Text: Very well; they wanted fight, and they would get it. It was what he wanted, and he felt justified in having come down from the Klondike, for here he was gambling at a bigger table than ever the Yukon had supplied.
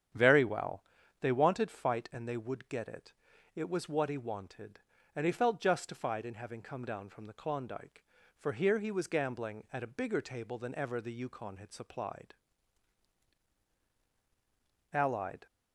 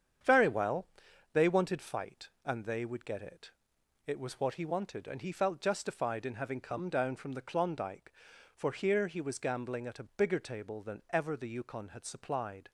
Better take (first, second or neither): second